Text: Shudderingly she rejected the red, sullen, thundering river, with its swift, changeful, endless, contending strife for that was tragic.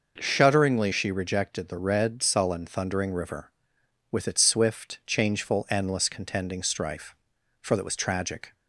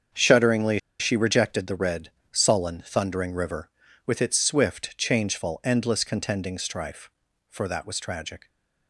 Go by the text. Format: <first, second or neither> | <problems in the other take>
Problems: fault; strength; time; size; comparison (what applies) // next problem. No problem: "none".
first | starts louder than the rest; strong; until 1.3 s; 7 dB // pauses between "Shudderingly" and "she"; slight; at 0.7 s; 0.21 s long